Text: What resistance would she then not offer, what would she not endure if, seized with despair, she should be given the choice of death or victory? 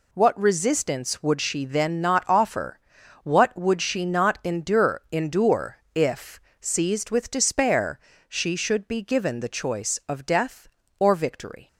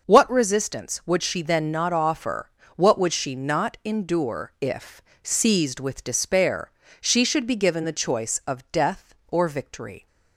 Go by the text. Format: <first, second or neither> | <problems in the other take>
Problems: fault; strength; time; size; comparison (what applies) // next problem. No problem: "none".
second | says "endure" twice; at 5.1 s